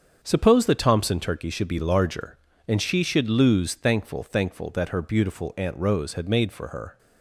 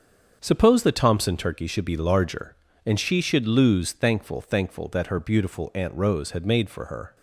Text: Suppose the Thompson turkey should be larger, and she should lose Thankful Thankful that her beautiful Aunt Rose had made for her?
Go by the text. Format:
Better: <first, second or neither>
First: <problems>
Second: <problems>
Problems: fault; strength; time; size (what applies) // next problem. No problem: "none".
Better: neither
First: starts louder than the rest; strong; until 1.2 s; 7 dB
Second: starts louder than the rest; strong; until 1.4 s; 7 dB